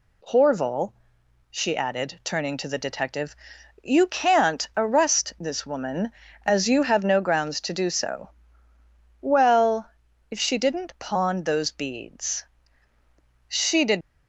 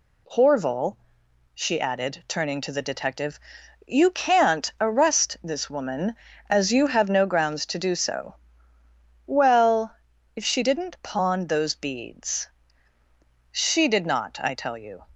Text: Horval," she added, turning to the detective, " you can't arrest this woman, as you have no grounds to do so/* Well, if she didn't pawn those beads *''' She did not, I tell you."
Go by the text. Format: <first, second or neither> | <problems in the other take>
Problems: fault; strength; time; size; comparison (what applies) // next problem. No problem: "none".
second | stops before "not I tell you"; at 14.0 s